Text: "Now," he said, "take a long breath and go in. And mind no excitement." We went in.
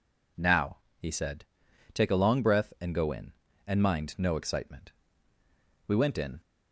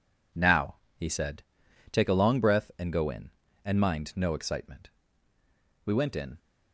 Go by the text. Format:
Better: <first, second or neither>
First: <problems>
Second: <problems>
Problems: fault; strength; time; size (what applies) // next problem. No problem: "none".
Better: first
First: none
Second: gets quieter; strong; throughout; 8 dB